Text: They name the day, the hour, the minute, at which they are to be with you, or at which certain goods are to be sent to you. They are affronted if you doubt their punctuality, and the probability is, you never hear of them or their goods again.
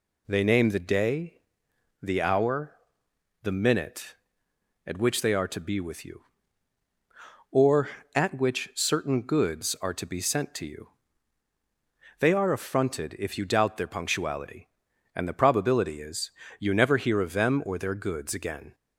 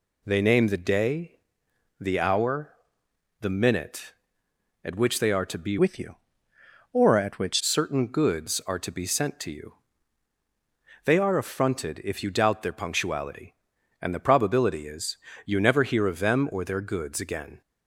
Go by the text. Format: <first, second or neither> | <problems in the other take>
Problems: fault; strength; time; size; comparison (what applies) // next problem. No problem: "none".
first | changes voice from "with" to "which"; from 5.7 to 7.6 s; 1.9 s long